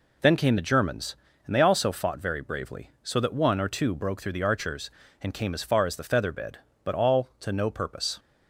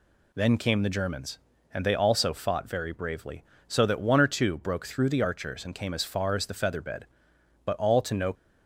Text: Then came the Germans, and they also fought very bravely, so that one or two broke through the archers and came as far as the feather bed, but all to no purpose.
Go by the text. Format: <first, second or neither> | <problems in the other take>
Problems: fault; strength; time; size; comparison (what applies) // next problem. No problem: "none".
first | stops before "purpose"; at 8.3 s